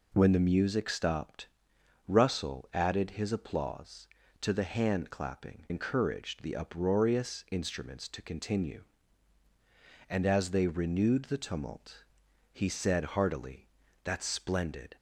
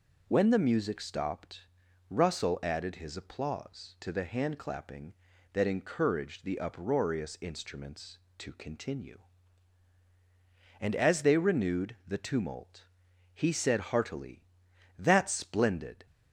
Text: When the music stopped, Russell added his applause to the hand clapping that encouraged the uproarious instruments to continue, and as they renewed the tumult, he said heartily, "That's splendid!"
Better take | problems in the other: second | skips "that"; at 5.6 s

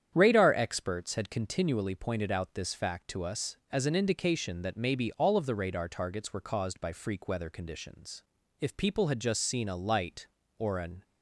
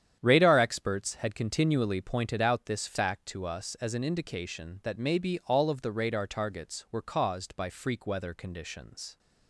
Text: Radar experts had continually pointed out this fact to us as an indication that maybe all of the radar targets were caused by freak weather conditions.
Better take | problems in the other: second | starts louder than the rest; strong; until 1.1 s; 9 dB; strong in the second // goes on to say "If people had just seen a light or an"; strong; from 8.6 s on; 2.4 s long

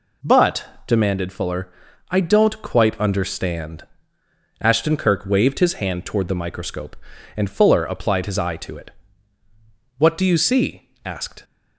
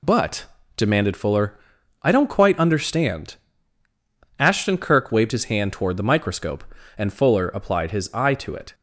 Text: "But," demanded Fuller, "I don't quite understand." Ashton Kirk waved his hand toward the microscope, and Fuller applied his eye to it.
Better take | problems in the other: second | goes on to say "What do you see asked"; from 9.9 s on; 1.4 s long

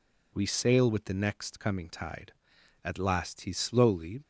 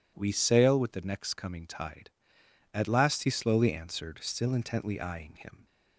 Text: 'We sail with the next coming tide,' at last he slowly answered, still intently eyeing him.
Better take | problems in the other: second | stops before "answered still intently eyeing him"; at 4.2 s

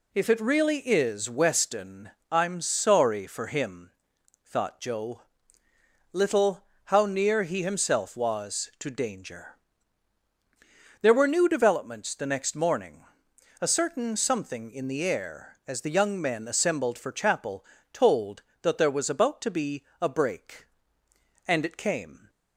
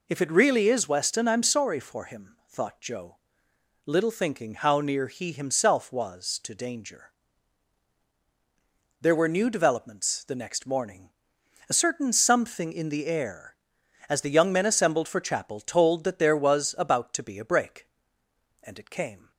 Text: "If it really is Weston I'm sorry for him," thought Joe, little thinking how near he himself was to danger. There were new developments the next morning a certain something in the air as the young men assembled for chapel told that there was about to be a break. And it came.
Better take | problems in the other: second | pauses between "Weston" and "I'm"; slight; at 2.0 s; 0.22 s long // skips "thinking"; at 6.7 s // pauses between "morning" and "a"; noticeable; at 13.0 s; 0.58 s long; noticeable in the second // pauses between "chapel" and "told"; slight; at 17.6 s; 0.28 s long // pauses between "be" and "a"; slight; at 19.8 s; 0.18 s long

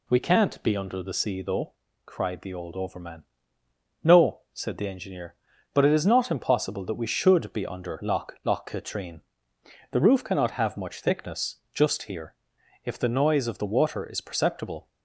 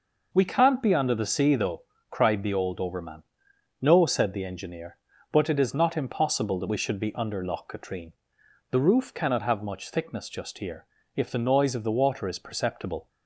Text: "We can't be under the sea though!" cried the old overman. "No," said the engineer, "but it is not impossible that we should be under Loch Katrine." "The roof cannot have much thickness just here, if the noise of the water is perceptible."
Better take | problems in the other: second | says "Loch" twice; at 8.4 s // pauses between "thickness" and "just"; slight; at 11.5 s; 0.18 s long

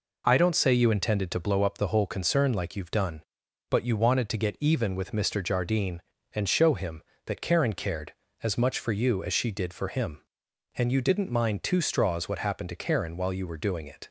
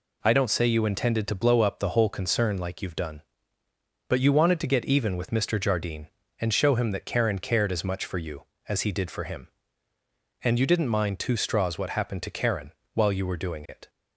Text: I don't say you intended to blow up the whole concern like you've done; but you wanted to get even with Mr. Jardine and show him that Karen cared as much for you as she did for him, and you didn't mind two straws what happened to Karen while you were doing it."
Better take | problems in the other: first | says "he" for "she"; at 8.8 s // pauses between "Karen" and "while"; slight; at 12.7 s; 0.20 s long

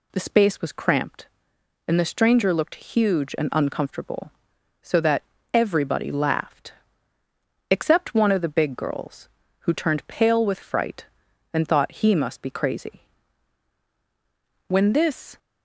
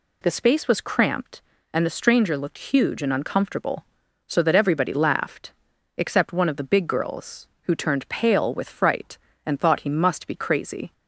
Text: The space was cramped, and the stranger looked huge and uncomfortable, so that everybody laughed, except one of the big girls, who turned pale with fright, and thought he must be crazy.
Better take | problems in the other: second | pauses between "that" and "everybody"; slight; at 5.2 s; 0.30 s long // goes on to say "When this"; noticeable; from 14.6 s on; 0.70 s long

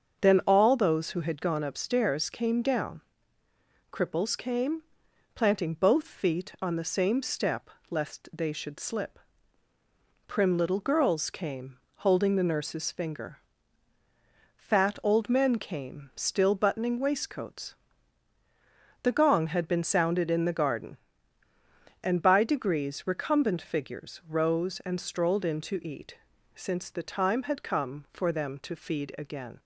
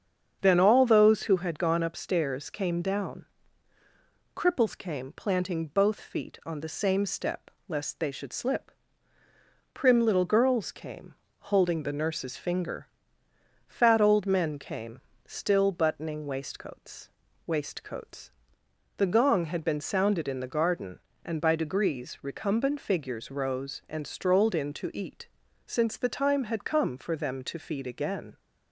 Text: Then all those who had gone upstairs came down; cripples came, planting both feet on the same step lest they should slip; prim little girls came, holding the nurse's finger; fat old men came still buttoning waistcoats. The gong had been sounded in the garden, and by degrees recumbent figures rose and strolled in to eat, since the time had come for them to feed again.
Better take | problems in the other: first | starts louder than the rest; strong; until 1.4 s; 7.5 dB; also in the first // pauses between "step" and "lest"; slight; at 7.5 s; 0.16 s long; slight in the first // pauses between "came" and "still"; slight; at 15.0 s; 0.24 s long // says "waistcoats" twice; at 17.4 s

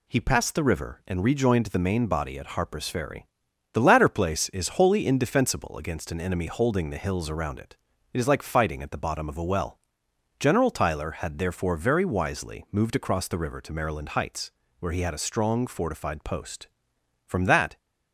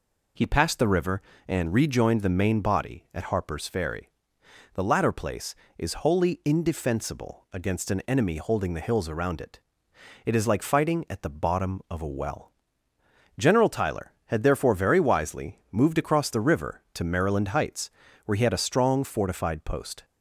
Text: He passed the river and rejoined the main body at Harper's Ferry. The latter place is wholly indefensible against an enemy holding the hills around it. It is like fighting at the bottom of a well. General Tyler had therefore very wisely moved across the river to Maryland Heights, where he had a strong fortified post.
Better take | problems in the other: second | goes on to say "From that"; from 17.2 s on; 0.52 s long

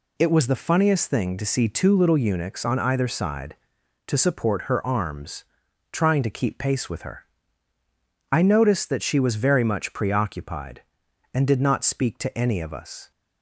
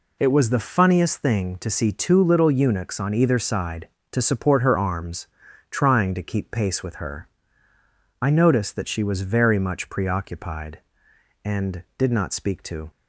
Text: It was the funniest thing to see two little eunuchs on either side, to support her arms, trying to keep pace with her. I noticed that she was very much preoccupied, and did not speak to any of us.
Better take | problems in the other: first | stops before "any of us"; at 12.9 s

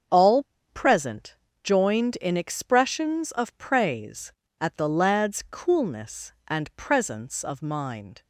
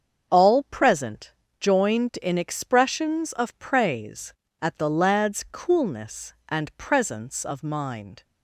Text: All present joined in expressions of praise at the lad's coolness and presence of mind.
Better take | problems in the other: second | starts louder than the rest; until 1.3 s; 7 dB; also in the second // pauses between "All" and "present"; slight; at 0.4 s; 0.24 s long // pauses between "present" and "joined"; slight; at 1.3 s; 0.30 s long; slight in the second

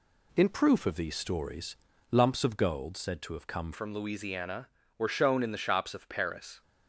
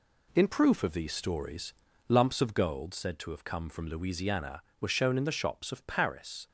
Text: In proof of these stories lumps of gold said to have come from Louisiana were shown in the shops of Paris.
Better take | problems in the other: second | pauses between "stories" and "lumps"; at 1.7 s; 0.38 s long; also in the second // changes voice at "from"; from 3.7 s on; 2.9 s long

